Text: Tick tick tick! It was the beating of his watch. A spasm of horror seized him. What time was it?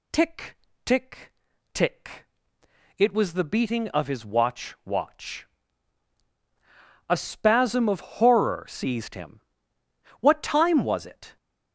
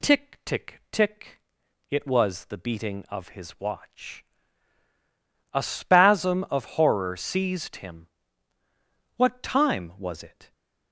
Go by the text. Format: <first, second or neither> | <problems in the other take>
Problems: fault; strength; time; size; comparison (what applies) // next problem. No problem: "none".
second | pauses between "Tick" and "tick"; slight; at 0.5 s; 0.28 s long // pauses between "tick" and "tick"; at 1.3 s; 0.42 s long // says "watch" twice; at 4.8 s